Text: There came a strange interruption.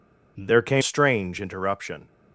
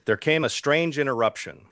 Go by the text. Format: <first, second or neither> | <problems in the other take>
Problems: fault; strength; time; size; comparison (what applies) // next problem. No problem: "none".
second | skips "a"; at 0.8 s